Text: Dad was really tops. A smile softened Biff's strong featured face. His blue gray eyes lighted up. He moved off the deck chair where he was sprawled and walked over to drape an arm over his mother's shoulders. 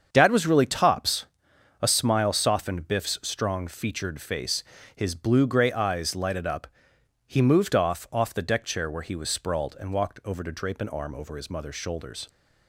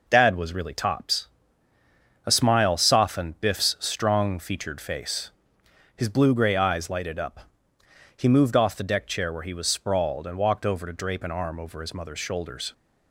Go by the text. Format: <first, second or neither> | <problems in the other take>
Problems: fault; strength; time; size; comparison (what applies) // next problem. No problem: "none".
second | starts louder than the rest; strong; until 1.1 s; 7 dB // says "off" twice; at 8.1 s